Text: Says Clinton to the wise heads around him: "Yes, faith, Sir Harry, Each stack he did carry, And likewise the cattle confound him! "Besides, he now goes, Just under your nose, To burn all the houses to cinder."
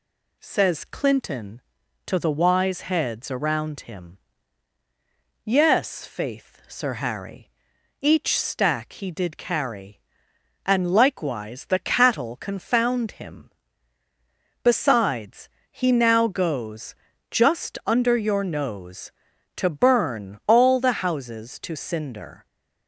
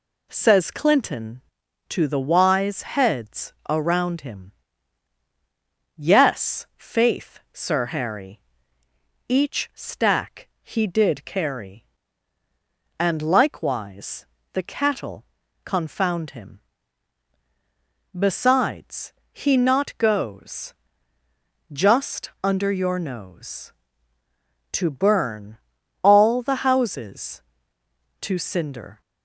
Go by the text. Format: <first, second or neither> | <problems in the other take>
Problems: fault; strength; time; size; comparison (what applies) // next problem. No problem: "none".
first | pauses between "likewise" and "the"; slight; at 14.2 s; 0.26 s long // pauses between "cattle" and "confound"; at 15.2 s; 0.40 s long // says "not" for "now"; at 19.5 s // pauses between "burn" and "all"; noticeable; at 25.5 s; 0.46 s long